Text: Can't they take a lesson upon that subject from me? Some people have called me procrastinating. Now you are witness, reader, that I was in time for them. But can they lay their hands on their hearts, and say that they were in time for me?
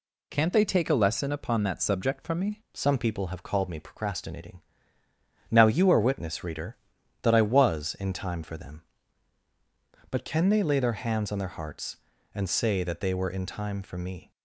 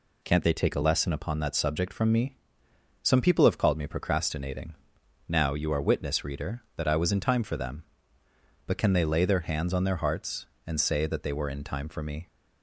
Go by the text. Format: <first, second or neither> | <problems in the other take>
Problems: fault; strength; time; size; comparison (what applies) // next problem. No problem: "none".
second | changes voice at "Some"; from 2.7 s on; 11.6 s long